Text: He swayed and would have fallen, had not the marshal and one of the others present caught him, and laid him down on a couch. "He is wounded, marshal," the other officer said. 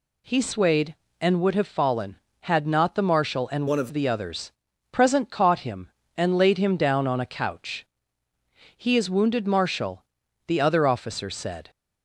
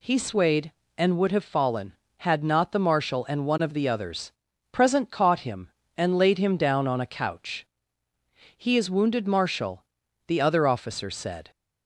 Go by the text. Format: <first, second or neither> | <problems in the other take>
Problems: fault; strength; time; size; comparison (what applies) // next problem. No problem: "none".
second | changes voice from "one" to "of"; from 3.6 to 3.8 s; 0.2 s long // pauses between "others" and "present"; at 4.5 s; 0.40 s long; also in the second